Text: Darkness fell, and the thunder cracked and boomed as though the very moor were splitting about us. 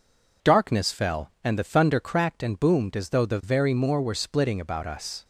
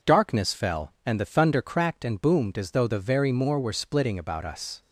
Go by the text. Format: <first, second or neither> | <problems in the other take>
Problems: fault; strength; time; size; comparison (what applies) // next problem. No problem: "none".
neither | none